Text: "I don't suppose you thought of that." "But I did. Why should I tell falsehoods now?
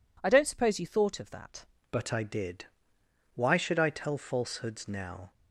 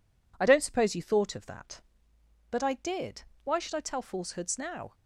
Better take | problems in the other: second | changes voice at "But"; from 1.9 s on; 3.4 s long

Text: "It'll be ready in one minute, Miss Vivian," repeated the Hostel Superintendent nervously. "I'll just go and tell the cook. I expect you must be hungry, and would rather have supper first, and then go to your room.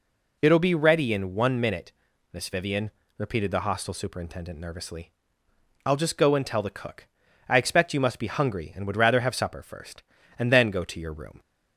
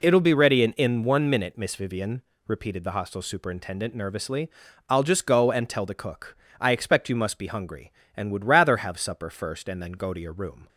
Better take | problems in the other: first | says "in" twice; at 0.7 s

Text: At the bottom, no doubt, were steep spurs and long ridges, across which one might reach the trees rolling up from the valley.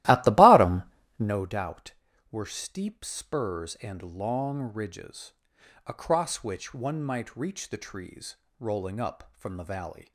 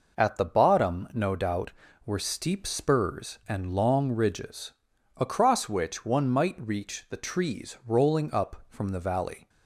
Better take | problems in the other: second | starts louder than the rest; strong; until 1.5 s; 16 dB // pauses between "trees" and "rolling"; slight; at 8.3 s; 0.24 s long

